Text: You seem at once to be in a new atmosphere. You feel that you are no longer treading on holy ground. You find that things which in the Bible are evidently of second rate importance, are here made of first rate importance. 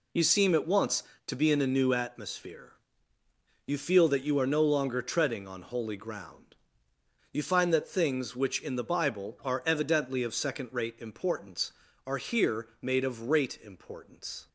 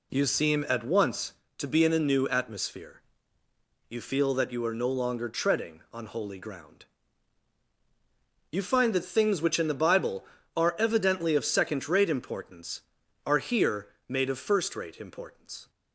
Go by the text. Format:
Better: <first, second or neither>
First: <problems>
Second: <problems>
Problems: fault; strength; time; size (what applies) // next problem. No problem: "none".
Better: second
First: pauses between "here" and "made"; slight; at 12.6 s; 0.16 s long // skips "first"; at 13.2 s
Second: pauses between "here" and "made"; slight; at 13.8 s; 0.22 s long